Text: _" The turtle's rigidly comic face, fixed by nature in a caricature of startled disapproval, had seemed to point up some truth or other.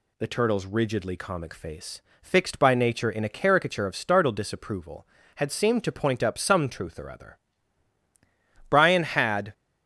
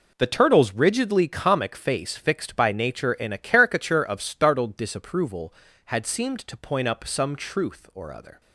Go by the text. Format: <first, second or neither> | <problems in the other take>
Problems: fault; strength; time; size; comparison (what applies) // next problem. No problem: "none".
second | goes on to say "Brian had"; noticeable; from 8.6 s on; 0.84 s long